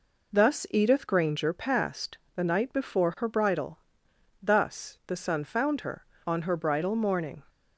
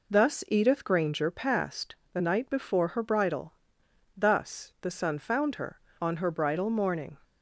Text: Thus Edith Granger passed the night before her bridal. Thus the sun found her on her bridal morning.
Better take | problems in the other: neither | pauses between "passed" and "the"; slight; the same in both

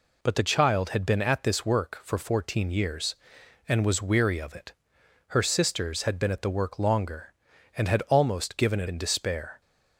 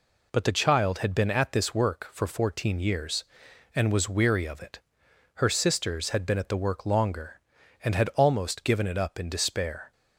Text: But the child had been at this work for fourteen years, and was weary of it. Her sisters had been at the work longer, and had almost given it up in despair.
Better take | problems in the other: second | skips "up"; at 8.8 s

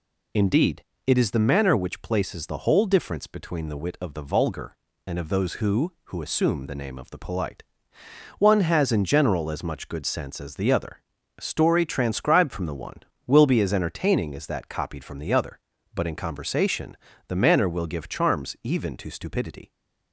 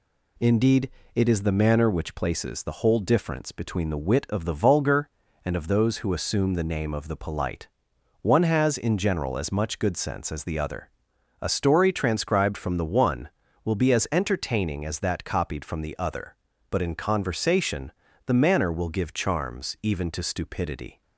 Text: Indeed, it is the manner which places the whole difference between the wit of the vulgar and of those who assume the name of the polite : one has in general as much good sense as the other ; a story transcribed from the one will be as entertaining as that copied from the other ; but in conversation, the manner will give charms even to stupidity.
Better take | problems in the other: second | says "who" twice; at 6.0 s

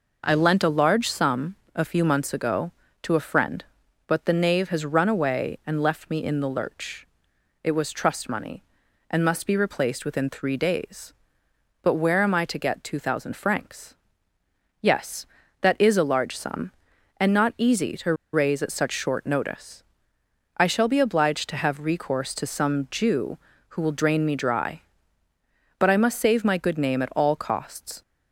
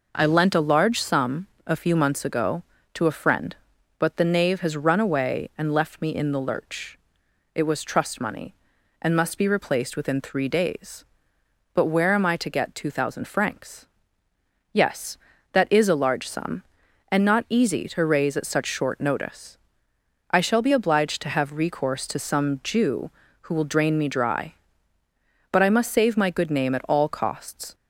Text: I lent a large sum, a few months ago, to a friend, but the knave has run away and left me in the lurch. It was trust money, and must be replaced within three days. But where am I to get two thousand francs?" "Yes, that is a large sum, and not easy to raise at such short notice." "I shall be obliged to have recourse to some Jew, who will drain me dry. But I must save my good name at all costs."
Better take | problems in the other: second | pauses between "to" and "raise"; slight; at 18.1 s; 0.18 s long

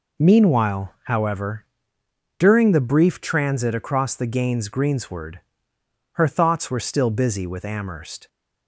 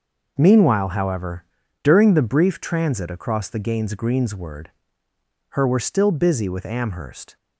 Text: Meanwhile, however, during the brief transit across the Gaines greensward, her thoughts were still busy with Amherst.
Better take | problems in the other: first | skips "thoughts"; at 5.6 s

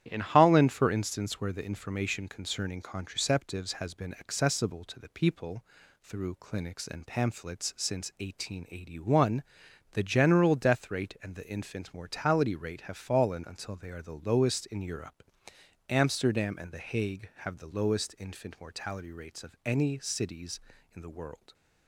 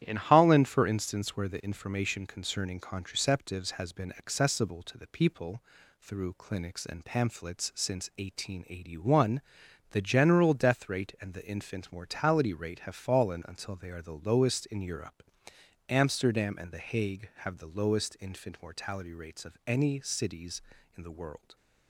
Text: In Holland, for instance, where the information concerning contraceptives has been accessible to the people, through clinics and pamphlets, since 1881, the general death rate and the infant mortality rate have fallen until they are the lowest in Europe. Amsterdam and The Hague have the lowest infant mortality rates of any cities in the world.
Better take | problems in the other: neither | starts louder than the rest; strong; the same in both

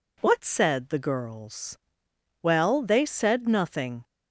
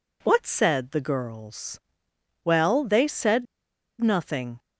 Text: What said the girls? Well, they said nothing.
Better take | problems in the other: first | pauses between "said" and "nothing"; noticeable; at 3.4 s; 0.56 s long

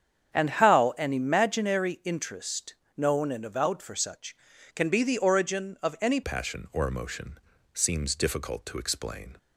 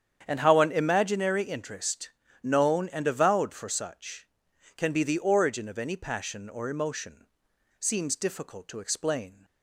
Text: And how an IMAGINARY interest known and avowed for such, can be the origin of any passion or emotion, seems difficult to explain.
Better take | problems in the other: second | starts louder than the rest; strong; until 1.3 s; 8.5 dB; strong in the second // pauses between "interest" and "known"; slight; at 2.7 s; 0.24 s long; slight in the second // changes voice at "passion"; from 6.2 s on; 3.1 s long

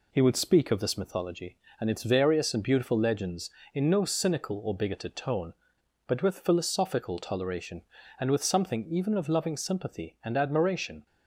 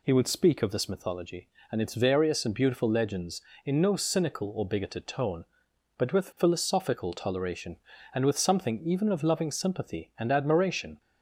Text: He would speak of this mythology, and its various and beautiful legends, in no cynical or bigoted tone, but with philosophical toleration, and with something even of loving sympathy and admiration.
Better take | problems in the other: second | gets quieter; throughout; 3.5 dB

